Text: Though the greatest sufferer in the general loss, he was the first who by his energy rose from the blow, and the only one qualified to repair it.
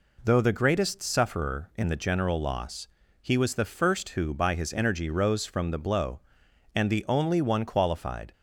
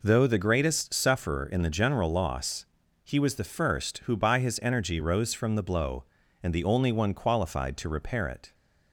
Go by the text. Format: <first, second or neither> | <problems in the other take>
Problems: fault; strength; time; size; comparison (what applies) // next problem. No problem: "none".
second | stops before "to repair it"; at 8.3 s